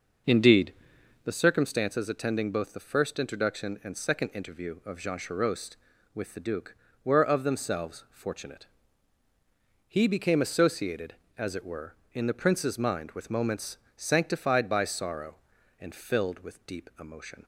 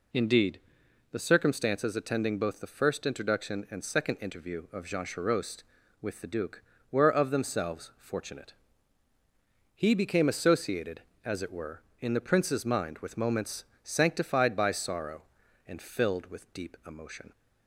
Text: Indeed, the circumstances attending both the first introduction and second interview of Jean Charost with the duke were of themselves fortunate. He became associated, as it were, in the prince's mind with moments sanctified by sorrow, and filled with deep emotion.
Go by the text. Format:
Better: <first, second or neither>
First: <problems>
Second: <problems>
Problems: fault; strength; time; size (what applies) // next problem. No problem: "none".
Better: second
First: starts louder than the rest; noticeable; until 1.4 s; 6 dB // pauses between "moments" and "sanctified"; slight; at 13.7 s; 0.18 s long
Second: pauses between "moments" and "sanctified"; slight; at 13.6 s; 0.18 s long